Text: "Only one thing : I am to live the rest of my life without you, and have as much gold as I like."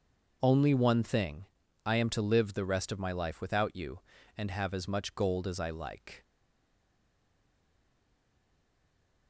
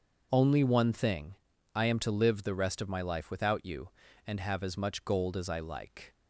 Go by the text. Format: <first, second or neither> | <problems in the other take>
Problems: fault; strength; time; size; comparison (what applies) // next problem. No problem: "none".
second | starts louder than the rest; until 1.4 s; 6.5 dB; also in the second // stays silent after the last word; strong; from 6.2 s on; 3.0 s long